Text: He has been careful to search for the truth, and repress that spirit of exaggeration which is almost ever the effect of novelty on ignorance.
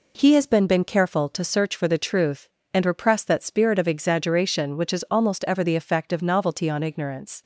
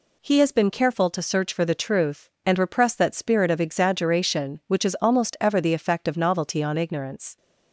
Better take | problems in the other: second | says "been" twice; at 0.6 s

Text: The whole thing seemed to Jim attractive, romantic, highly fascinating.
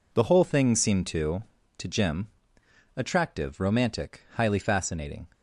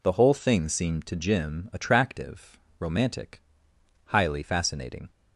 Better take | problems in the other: second | says "to" twice; at 1.7 s // pauses between "Jim" and "attractive"; noticeable; at 2.2 s; 0.70 s long

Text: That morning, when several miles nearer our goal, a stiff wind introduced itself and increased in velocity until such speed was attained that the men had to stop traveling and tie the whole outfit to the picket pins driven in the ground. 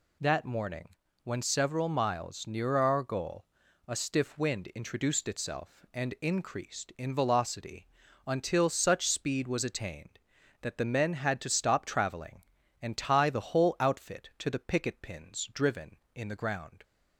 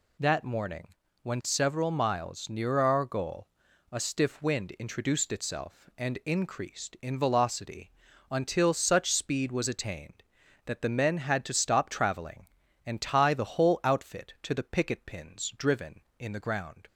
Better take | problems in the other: neither | pauses between "velocity" and "until"; the same in both

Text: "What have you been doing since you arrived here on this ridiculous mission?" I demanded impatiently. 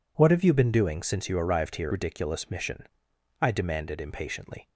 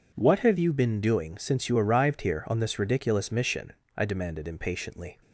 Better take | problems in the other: second | skips "on this"; at 1.9 s

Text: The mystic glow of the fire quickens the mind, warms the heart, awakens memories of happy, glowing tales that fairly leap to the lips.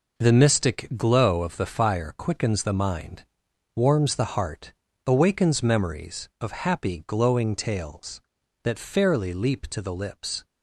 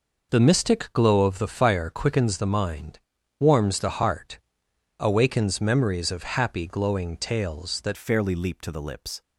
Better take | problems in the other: first | changes voice at "fairly"; from 7.9 s on; 1.3 s long

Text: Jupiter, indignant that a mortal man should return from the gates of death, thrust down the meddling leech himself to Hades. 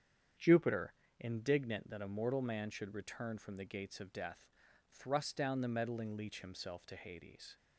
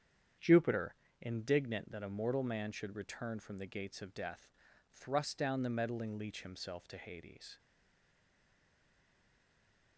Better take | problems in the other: first | starts louder than the rest; strong; until 1.6 s; 8 dB; strong in the first // stays silent after the last word; from 7.5 s on; 2.4 s long

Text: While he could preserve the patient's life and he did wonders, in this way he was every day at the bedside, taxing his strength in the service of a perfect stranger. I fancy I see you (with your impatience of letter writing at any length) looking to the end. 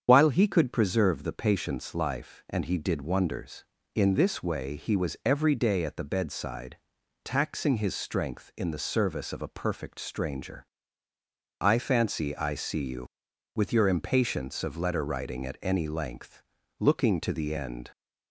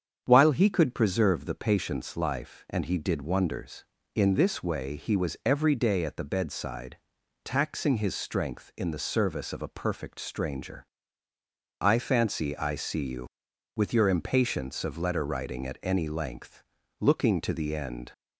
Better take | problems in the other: second | loses the start of "While"; at 0.0 s; 55 ms // starts louder than the rest; strong; until 1.0 s; 8 dB; strong in the second

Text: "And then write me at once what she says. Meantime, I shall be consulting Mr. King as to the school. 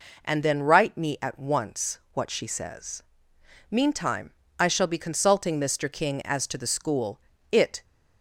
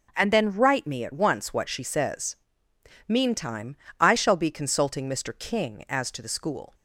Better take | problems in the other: second | goes on to say "It"; slight; from 7.5 s on; 0.32 s long

